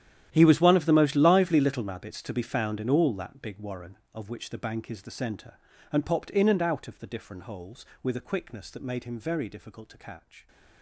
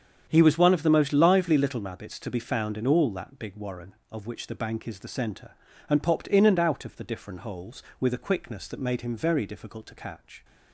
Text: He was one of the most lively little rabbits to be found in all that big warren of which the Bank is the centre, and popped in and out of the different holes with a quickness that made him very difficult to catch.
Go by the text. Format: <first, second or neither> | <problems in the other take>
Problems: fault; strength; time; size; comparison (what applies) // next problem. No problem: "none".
second | gets quieter; strong; throughout; 18 dB // starts louder than the rest; strong; until 1.3 s; 11.5 dB; strong in the second